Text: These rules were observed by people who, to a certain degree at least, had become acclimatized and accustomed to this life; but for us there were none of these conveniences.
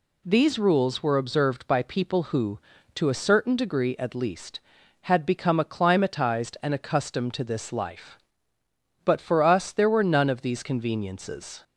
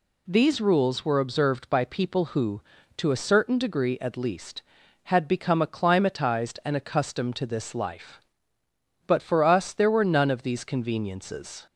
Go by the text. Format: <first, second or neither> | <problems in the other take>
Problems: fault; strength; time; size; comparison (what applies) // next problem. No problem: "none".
neither | none